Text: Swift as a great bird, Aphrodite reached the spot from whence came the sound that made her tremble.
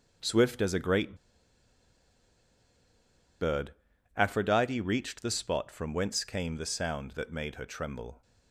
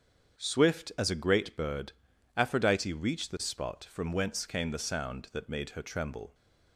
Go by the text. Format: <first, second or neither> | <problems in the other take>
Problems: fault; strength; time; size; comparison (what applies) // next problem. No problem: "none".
second | starts louder than the rest; until 3.4 s; 6.5 dB; strong in the second // pauses between "great" and "bird"; strong; at 1.1 s; 2.2 s long